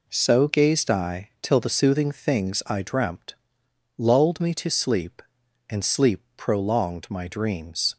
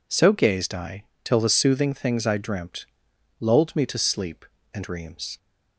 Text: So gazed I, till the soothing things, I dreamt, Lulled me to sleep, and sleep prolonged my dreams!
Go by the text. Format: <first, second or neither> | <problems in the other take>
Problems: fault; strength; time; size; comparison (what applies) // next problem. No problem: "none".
first | skips "sleep prolonged my"; at 4.8 s